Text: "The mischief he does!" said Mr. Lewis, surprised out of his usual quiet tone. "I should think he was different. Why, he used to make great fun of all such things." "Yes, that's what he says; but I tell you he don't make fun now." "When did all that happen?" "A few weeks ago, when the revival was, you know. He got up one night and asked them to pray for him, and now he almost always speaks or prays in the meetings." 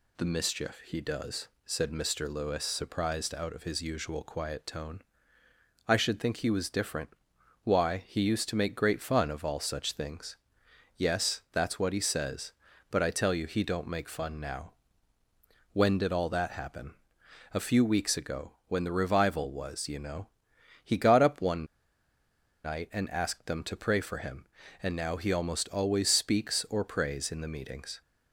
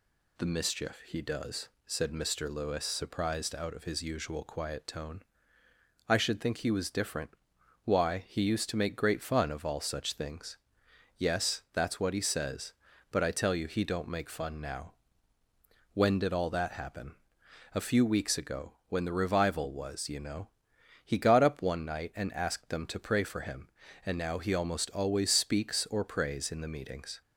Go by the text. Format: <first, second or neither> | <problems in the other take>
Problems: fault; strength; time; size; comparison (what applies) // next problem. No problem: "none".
second | pauses between "one" and "night"; at 21.6 s; 0.99 s long